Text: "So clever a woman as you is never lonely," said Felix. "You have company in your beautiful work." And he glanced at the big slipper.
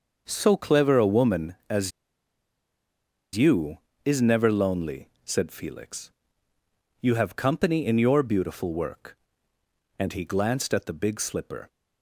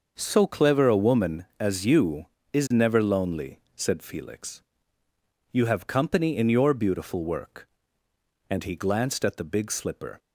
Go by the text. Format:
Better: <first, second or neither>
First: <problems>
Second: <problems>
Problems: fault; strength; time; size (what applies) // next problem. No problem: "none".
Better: second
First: starts louder than the rest; until 1.2 s; 6 dB // pauses between "as" and "you"; strong; at 1.9 s; 1.4 s long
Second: starts louder than the rest; until 1.1 s; 6 dB